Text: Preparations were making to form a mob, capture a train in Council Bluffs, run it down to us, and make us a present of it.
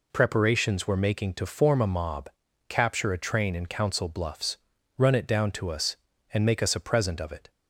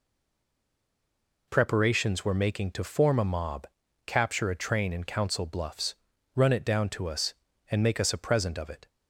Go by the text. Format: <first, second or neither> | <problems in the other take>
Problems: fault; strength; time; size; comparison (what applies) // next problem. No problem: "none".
first | stays silent before the first word; noticeable; until 1.4 s; 1.4 s long